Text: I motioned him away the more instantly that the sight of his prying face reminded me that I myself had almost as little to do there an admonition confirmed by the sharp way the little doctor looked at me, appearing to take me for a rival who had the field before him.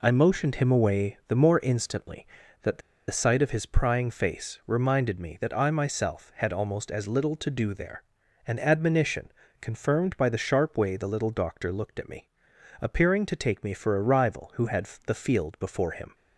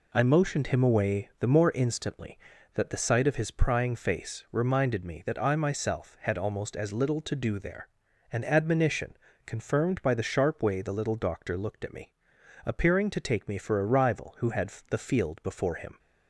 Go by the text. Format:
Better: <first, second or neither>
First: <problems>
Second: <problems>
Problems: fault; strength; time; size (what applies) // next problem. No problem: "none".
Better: second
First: pauses between "the" and "sight"; slight; at 2.8 s; 0.29 s long // pauses between "there" and "an"; at 8.0 s; 0.44 s long // pauses between "admonition" and "confirmed"; slight; at 9.3 s; 0.26 s long // pauses between "had" and "the"; slight; at 14.8 s; 0.18 s long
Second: pauses between "there" and "an"; at 7.8 s; 0.44 s long // pauses between "admonition" and "confirmed"; slight; at 9.1 s; 0.26 s long // pauses between "had" and "the"; slight; at 14.7 s; 0.18 s long